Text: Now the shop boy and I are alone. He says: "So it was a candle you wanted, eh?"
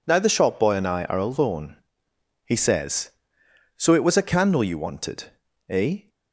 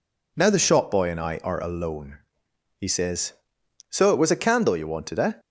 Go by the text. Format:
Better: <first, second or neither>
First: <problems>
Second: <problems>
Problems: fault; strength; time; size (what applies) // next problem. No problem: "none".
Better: neither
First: none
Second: none